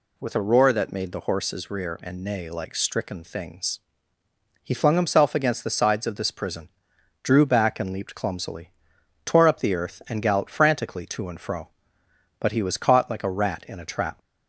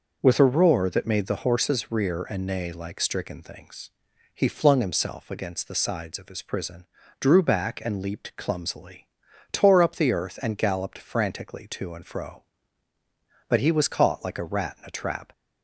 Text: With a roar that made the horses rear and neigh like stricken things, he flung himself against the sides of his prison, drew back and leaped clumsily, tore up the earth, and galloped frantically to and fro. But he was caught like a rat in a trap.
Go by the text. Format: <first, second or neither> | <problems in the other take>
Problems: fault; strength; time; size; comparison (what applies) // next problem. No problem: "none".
second | says "this" for "his"; at 6.1 s